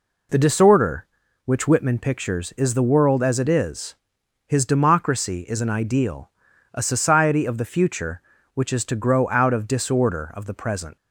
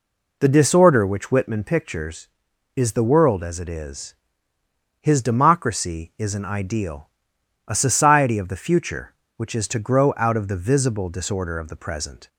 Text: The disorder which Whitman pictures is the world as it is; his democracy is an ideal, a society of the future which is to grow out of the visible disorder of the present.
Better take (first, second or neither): second